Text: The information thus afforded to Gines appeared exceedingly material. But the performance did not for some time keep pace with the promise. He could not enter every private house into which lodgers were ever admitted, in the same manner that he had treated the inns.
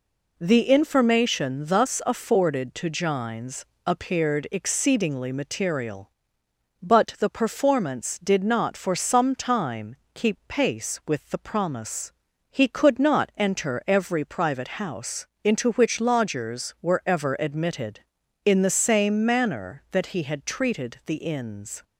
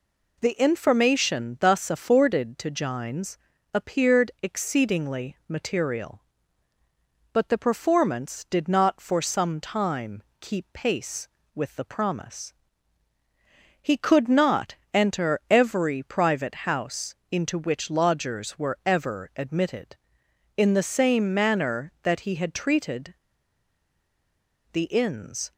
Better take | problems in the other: first | pauses between "Gines" and "appeared"; slight; at 3.3 s; 0.36 s long; slight in the first // pauses between "time" and "keep"; slight; at 10.2 s; 0.18 s long; slight in the first // pauses between "not" and "enter"; slight; at 14.7 s; 0.18 s long // pauses between "house" and "into"; slight; at 17.1 s; 0.16 s long; slight in the first // pauses between "treated" and "the"; strong; at 23.1 s; 1.5 s long

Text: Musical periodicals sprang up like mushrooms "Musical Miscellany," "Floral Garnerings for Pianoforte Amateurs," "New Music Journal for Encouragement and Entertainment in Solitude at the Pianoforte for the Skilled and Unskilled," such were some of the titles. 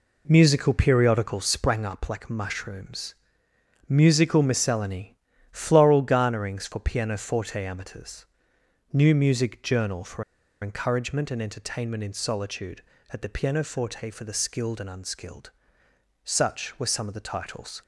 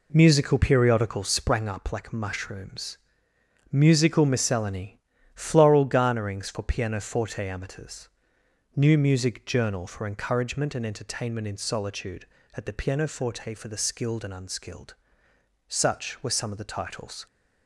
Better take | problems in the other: second | pauses between "mushrooms" and "Musical"; noticeable; at 3.1 s; 0.74 s long; noticeable in the second // pauses between "for" and "Encouragement"; at 10.2 s; 0.38 s long

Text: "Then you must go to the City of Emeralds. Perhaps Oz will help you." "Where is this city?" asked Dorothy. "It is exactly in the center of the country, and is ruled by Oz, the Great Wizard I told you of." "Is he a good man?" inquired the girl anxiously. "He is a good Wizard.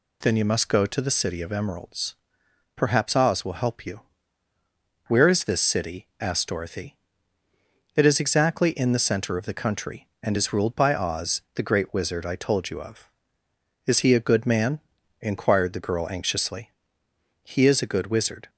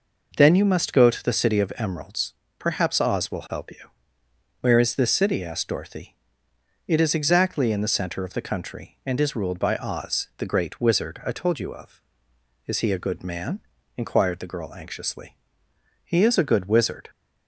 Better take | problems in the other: neither | none

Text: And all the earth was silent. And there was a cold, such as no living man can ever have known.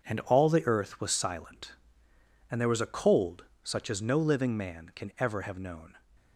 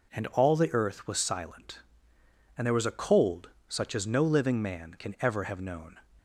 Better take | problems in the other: second | gets quieter; strong; throughout; 7.5 dB

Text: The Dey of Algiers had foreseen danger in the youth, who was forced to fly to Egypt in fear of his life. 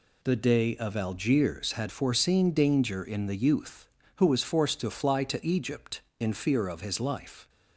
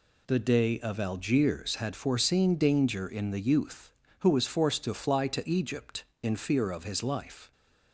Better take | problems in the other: neither | none

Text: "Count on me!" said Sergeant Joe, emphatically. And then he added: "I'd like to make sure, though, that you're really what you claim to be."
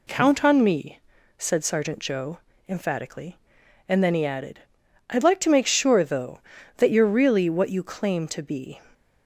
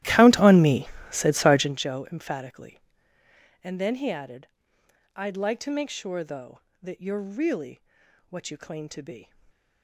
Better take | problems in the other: first | starts louder than the rest; strong; until 1.9 s; 14.5 dB // pauses between "really" and "what"; noticeable; at 7.8 s; 0.48 s long // stays silent after the last word; slight; from 9.2 s on; 0.6 s long

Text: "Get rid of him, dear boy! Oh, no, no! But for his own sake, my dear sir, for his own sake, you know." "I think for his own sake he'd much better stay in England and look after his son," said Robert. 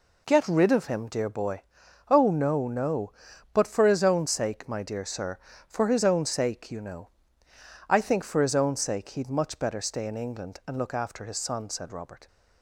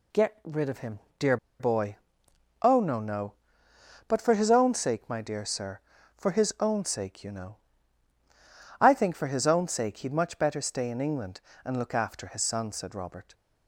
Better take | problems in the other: first | pauses between "dear" and "boy"; slight; at 1.3 s; 0.23 s long

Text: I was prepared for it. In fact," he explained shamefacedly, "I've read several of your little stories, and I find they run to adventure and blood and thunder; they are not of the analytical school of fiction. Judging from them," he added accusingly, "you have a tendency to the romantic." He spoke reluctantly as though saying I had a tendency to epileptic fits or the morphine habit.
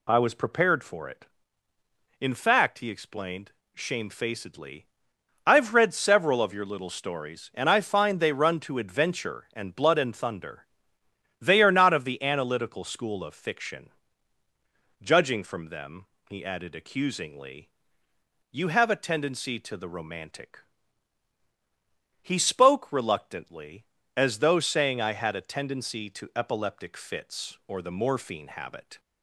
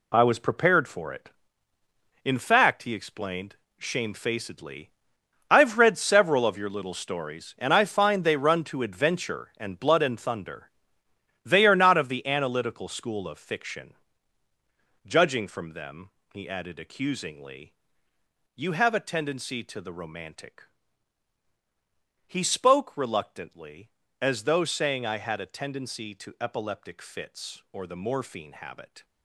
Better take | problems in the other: first | gets quieter; strong; throughout; 9.5 dB // pauses between "explained" and "shamefacedly"; slight; at 3.5 s; 0.22 s long; slight in the first

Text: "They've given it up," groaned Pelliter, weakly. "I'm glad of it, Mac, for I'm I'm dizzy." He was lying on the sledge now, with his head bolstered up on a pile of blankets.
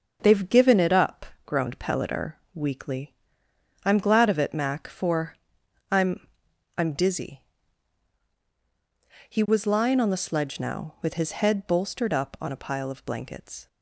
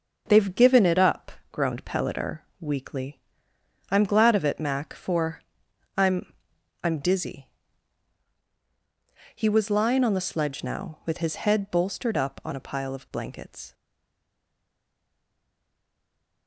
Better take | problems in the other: first | starts louder than the rest; until 1.2 s; 6.5 dB; also in the first // pauses between "for" and "I'm"; noticeable; at 5.4 s; 0.56 s long; noticeable in the first // pauses between "I'm" and "I'm"; noticeable; at 6.3 s; 0.50 s long; noticeable in the first // stays silent after the last word; strong; from 13.7 s on; 2.7 s long

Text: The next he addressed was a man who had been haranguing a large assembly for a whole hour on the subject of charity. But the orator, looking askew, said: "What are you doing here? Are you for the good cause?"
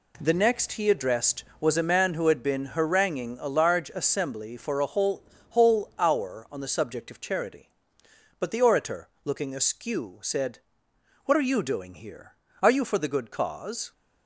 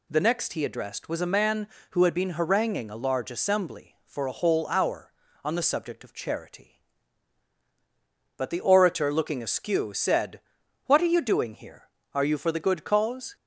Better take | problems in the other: second | says "whole" twice; at 5.4 s

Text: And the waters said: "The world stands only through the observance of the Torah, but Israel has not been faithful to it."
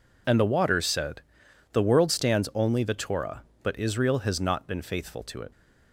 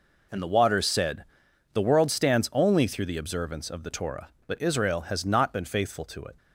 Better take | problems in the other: second | skips "through the observance of"; at 2.8 s

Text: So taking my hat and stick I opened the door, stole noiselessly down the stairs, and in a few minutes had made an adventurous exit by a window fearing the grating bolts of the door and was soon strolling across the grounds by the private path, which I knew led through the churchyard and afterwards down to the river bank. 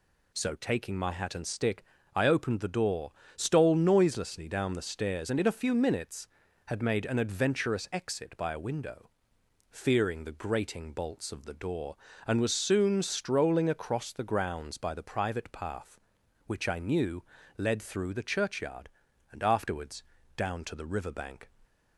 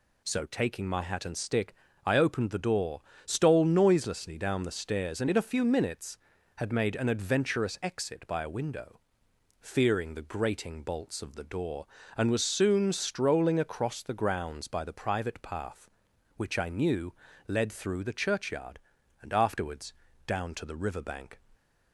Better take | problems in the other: neither | pauses between "stick" and "I"; slight; the same in both // pauses between "window" and "fearing"; noticeable; the same in both // pauses between "knew" and "led"; slight; the same in both // pauses between "afterwards" and "down"; slight; the same in both

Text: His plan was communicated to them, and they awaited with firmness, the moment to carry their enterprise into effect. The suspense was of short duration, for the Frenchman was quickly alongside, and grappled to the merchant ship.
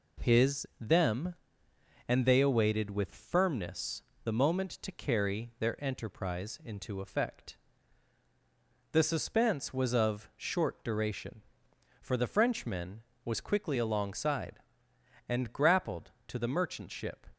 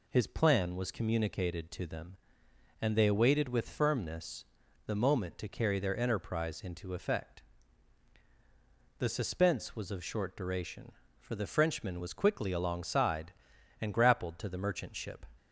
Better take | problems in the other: second | skips "plan was communicated to"; at 0.7 s

